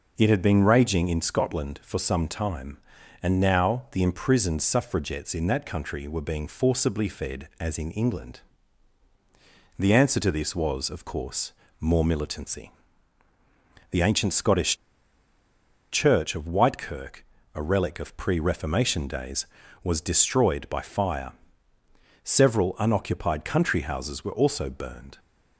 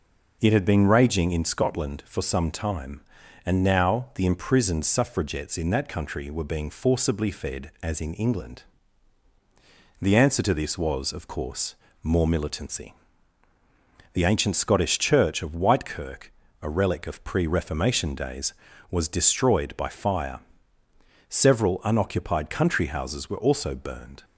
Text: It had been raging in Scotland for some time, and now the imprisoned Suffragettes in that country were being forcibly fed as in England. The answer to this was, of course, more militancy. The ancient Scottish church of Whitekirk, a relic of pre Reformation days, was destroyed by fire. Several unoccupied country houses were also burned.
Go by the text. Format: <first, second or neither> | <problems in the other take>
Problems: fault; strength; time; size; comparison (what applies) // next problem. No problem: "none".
second | pauses between "Scottish" and "church"; at 14.7 s; 1.1 s long